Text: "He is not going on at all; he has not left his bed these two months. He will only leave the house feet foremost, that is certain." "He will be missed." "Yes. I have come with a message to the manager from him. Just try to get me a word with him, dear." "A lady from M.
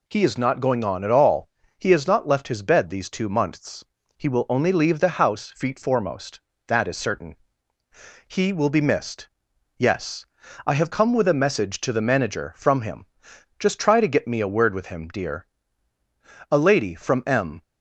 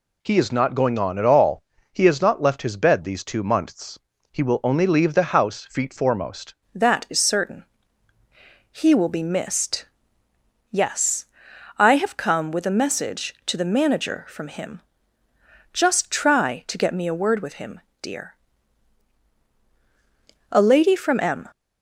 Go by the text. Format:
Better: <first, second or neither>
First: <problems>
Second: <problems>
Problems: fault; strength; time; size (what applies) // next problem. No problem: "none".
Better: first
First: none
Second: changes voice at "that"; from 6.7 s on; 14.7 s long